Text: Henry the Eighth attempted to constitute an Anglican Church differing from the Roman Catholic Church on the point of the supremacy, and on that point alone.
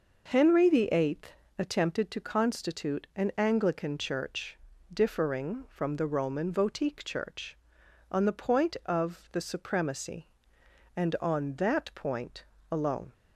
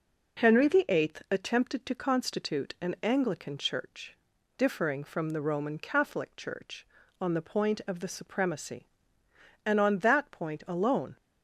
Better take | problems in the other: second | pauses between "Eighth" and "attempted"; slight; at 1.3 s; 0.20 s long // pauses between "Church" and "differing"; slight; at 4.5 s; 0.34 s long; also in the second // says "Votique" for "Catholic"; at 6.5 s // pauses between "point" and "alone"; slight; at 12.4 s; 0.30 s long

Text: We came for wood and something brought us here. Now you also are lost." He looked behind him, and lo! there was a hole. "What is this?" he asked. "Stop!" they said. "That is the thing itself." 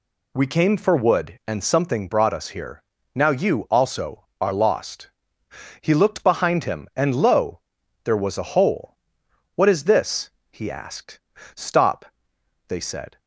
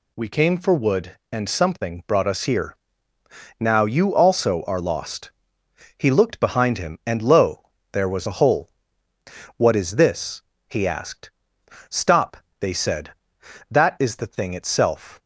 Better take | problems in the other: second | stops before "That is the thing itself"; at 13.1 s

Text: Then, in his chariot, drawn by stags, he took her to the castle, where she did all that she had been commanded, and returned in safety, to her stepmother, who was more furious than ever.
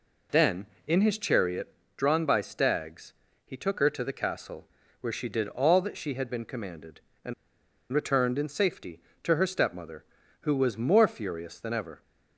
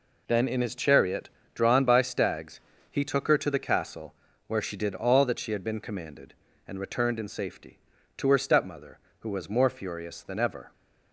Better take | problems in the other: second | pauses between "and" and "returned"; noticeable; at 7.3 s; 0.59 s long

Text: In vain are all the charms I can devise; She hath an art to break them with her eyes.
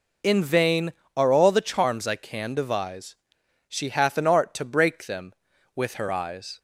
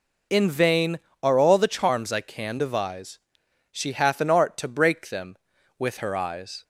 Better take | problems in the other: neither | none

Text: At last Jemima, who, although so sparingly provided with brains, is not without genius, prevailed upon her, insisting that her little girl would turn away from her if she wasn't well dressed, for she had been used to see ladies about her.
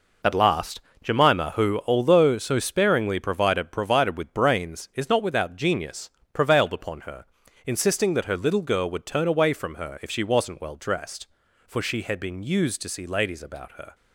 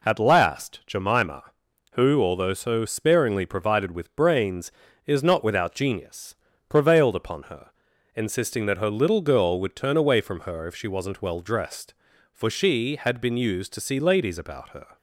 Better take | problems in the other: second | pauses between "last" and "Jemima"; slight; at 0.8 s; 0.22 s long // says "provided" twice; at 3.7 s

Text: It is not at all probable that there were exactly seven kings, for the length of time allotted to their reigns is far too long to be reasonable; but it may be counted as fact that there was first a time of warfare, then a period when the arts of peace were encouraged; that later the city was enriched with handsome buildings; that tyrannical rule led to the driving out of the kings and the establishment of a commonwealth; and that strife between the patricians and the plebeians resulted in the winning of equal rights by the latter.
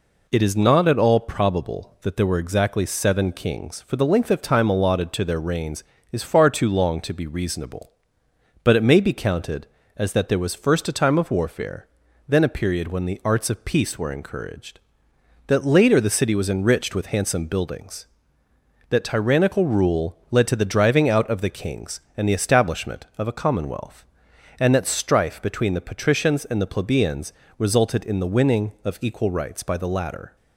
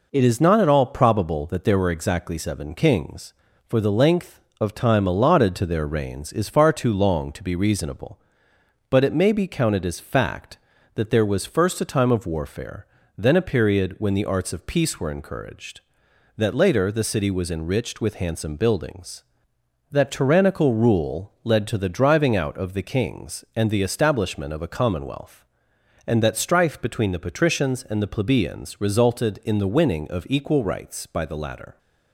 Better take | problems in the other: second | skips "fact"; at 10.1 s // pauses between "rule" and "led"; slight; at 20.1 s; 0.16 s long // pauses between "plebeians" and "resulted"; slight; at 27.3 s; 0.26 s long

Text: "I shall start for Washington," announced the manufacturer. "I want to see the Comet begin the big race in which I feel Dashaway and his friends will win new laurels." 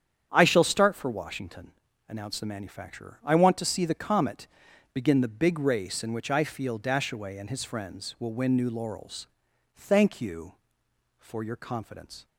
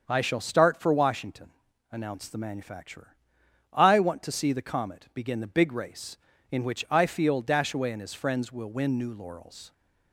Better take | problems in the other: second | starts louder than the rest; strong; until 1.3 s; 8.5 dB; also in the second // pauses between "Comet" and "begin"; noticeable; at 4.4 s; 0.48 s long // goes on to say "Thank you for your confidence"; strong; from 9.7 s on; 2.5 s long

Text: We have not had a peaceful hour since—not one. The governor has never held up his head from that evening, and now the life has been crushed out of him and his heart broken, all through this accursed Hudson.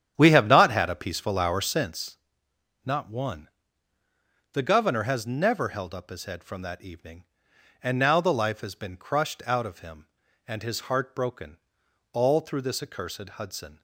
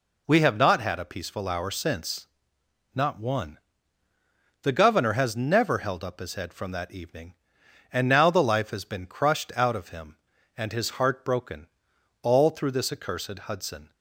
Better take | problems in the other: second | starts louder than the rest; strong; until 1.9 s; 9.5 dB

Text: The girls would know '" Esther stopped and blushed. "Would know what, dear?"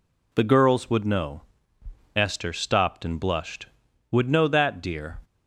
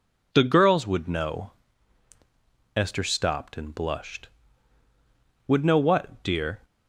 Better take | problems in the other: second | says "that" for "what"; at 4.4 s

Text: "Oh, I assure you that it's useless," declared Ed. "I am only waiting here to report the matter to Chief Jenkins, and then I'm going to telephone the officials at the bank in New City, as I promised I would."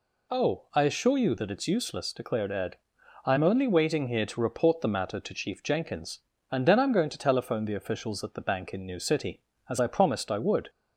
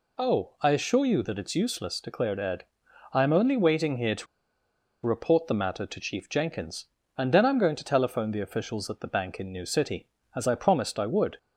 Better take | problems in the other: first | pauses between "to" and "report"; noticeable; at 4.2 s; 0.79 s long

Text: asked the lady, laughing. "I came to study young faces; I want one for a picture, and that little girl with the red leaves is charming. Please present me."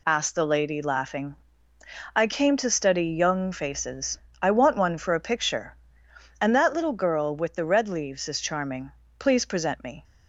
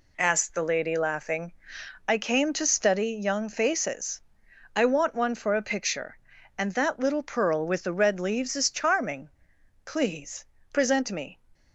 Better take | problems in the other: first | says "pearl" for "girl"; at 7.2 s // pauses between "Please" and "present"; slight; at 10.4 s; 0.26 s long

